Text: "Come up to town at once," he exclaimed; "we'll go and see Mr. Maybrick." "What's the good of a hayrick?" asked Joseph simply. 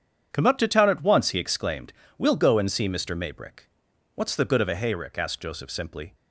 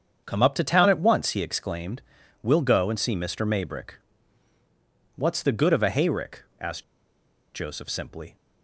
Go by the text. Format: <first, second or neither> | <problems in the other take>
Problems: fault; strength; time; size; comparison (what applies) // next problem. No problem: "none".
first | starts louder than the rest; strong; until 1.2 s; 7.5 dB; strong in the first // pauses between "asked" and "Joseph"; noticeable; at 6.8 s; 0.71 s long